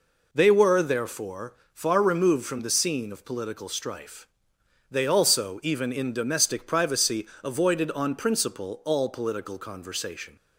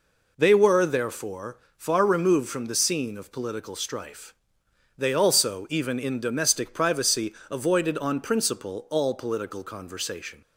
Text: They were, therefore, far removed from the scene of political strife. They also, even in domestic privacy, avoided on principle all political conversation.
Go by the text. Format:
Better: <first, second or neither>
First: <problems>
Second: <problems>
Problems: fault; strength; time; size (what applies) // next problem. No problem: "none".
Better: neither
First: none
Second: none